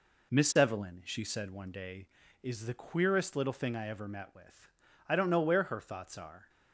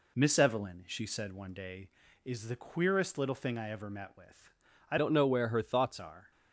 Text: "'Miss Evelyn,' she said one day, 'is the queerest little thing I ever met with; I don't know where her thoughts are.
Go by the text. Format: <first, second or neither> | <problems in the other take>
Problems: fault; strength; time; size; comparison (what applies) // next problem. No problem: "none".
first | changes voice from "don't" to "thoughts"; from 4.9 to 5.9 s; 1.0 s long